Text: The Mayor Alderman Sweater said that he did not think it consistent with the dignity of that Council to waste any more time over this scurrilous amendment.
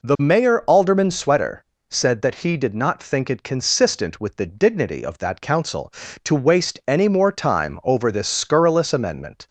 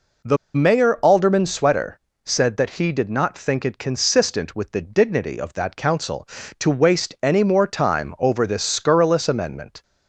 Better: first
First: pauses between "Sweater" and "said"; slight; at 1.6 s; 0.24 s long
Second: pauses between "The" and "Mayor"; slight; at 0.3 s; 0.19 s long // pauses between "Sweater" and "said"; slight; at 2.0 s; 0.24 s long

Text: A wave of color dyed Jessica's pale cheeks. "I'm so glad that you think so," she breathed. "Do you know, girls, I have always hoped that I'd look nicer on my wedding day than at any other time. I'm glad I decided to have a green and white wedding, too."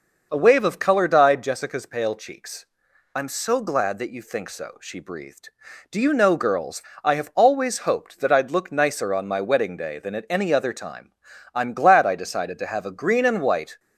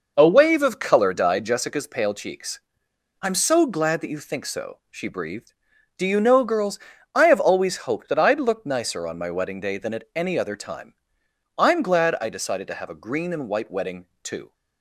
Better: second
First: stops before "wedding too"; at 13.7 s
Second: none

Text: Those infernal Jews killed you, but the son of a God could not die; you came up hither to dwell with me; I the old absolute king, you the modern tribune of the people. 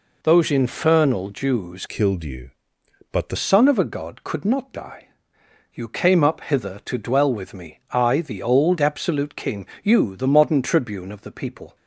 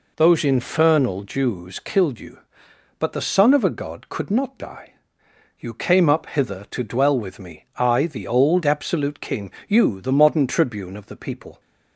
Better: second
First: changes voice from "killed" to "the"; from 1.8 to 3.3 s; 1.5 s long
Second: none

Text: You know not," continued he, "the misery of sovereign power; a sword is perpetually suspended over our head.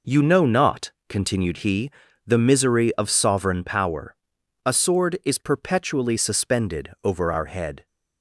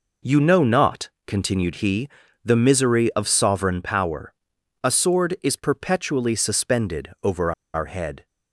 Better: first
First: none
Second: pauses between "over" and "our"; slight; at 7.5 s; 0.22 s long

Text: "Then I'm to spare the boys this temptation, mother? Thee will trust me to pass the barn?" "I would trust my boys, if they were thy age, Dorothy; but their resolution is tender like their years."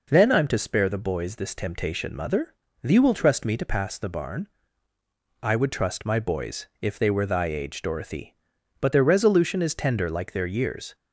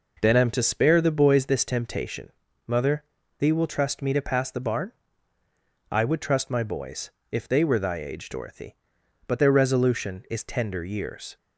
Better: first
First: none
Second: skips "like their"; at 10.8 s

